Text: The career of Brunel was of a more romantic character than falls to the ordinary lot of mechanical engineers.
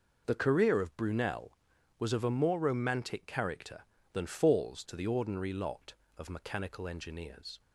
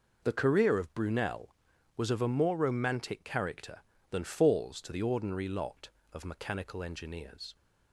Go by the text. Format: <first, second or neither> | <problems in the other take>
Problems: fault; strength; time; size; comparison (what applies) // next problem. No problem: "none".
neither | none